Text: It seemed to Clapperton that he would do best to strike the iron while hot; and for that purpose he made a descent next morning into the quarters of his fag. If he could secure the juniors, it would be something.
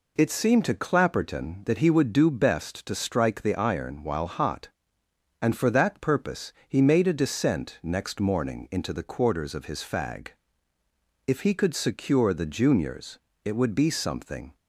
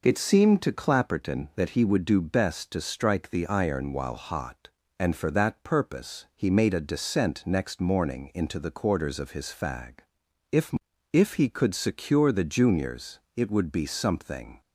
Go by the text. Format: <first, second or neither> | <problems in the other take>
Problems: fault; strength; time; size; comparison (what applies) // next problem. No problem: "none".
first | says "If" twice; at 11.1 s